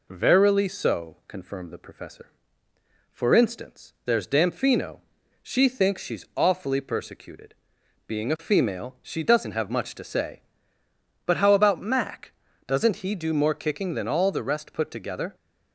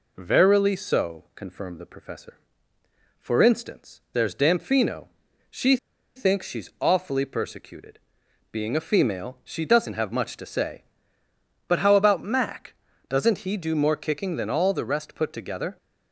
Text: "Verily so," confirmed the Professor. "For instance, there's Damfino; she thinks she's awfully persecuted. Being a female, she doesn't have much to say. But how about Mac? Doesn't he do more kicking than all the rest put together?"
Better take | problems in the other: first | pauses between "she" and "thinks"; at 5.7 s; 0.39 s long

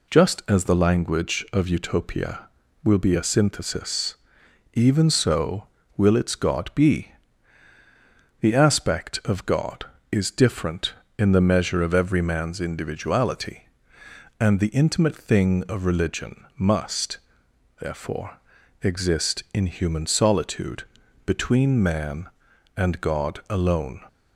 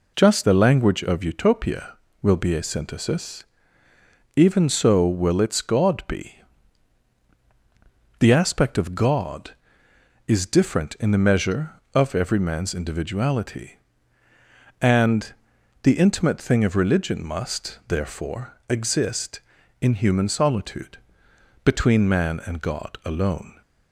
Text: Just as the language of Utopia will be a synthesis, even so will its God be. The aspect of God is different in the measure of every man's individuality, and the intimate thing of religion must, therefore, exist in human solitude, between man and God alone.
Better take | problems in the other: first | skips "as"; at 0.4 s // pauses between "and" and "the"; noticeable; at 15.3 s; 0.48 s long

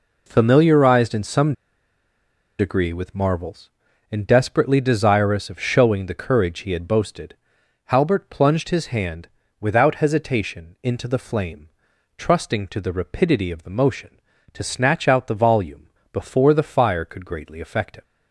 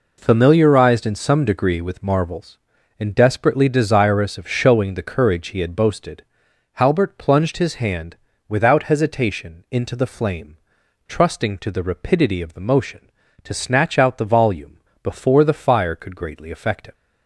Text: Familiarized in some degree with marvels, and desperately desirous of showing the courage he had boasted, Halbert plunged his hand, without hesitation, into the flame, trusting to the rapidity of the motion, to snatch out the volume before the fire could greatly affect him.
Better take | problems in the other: second | pauses between "some" and "degree"; at 1.5 s; 1.0 s long // pauses between "volume" and "before"; slight; at 15.8 s; 0.24 s long; slight in the second

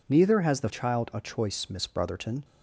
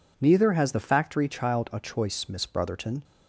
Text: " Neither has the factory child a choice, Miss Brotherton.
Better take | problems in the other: second | skips "factory"; at 0.6 s

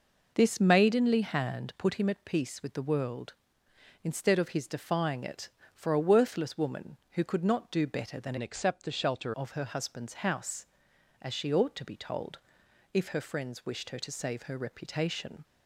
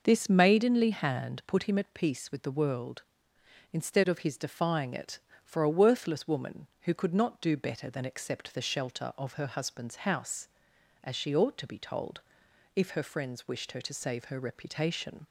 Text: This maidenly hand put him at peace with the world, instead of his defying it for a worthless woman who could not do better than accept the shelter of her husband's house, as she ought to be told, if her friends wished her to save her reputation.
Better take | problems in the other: second | changes voice from "accept" to "shelter"; from 8.3 to 9.3 s; 1.0 s long

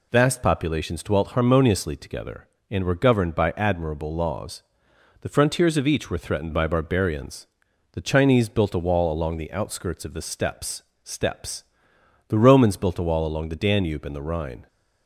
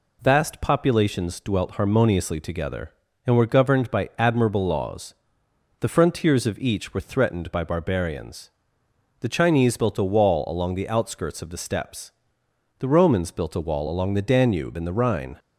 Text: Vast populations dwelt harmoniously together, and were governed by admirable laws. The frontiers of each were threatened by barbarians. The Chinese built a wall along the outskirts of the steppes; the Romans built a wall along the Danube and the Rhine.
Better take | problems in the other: second | says "steppes" twice; at 11.0 s

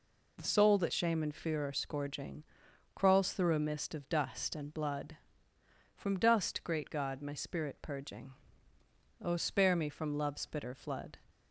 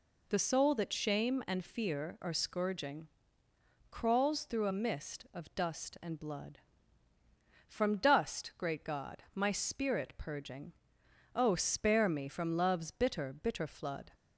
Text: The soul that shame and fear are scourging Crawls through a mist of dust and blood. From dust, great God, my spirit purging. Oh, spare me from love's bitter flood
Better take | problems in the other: first | pauses between "scourging" and "Crawls"; noticeable; at 3.0 s; 0.84 s long; noticeable in the first // says "bitter" twice; at 13.3 s

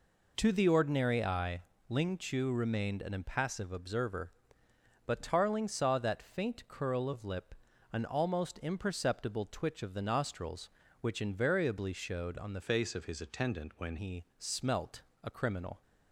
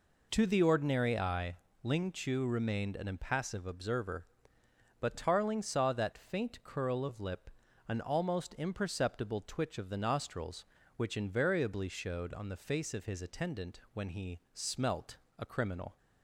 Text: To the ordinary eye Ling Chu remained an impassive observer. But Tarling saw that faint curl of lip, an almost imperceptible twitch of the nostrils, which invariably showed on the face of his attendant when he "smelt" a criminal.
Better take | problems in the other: second | pauses between "eye" and "Ling"; slight; at 1.6 s; 0.26 s long; slight in the second // changes voice from "face" to "when"; from 12.6 to 13.9 s; 1.3 s long // pauses between "he" and "smelt"; slight; at 14.2 s; 0.16 s long; slight in the second // pauses between "smelt" and "a"; slight; at 15.0 s; 0.20 s long; slight in the second

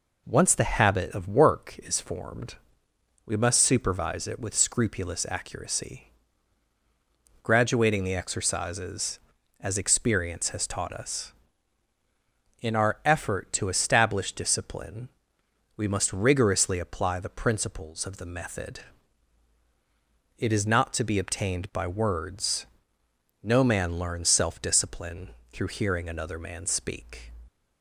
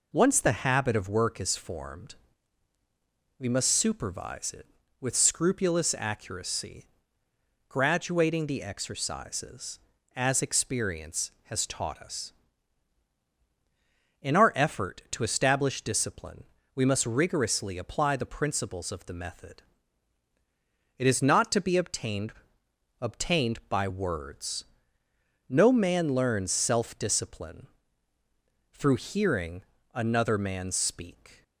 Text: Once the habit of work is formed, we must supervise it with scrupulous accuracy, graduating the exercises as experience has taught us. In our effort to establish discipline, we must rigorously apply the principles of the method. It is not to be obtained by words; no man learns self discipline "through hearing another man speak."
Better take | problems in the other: first | says "obtained" twice; at 22.9 s // pauses between "discipline" and "through"; at 27.6 s; 1.0 s long; slight in the first // pauses between "hearing" and "another"; slight; at 29.6 s; 0.32 s long

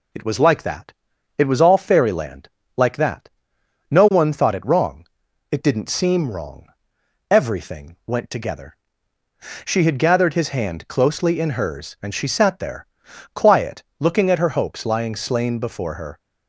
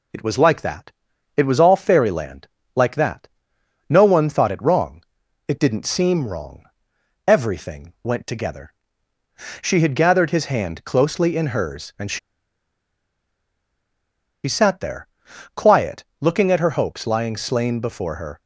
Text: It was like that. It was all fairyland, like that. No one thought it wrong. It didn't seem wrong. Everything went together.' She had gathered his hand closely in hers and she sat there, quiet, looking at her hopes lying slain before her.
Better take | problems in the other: first | pauses between "she" and "sat"; strong; at 12.1 s; 2.2 s long

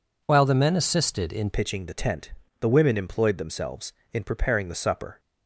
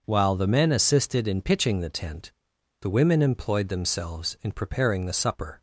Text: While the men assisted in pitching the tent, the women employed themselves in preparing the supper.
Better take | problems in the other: second | changes voice at "pitching"; from 1.5 s on; 3.6 s long

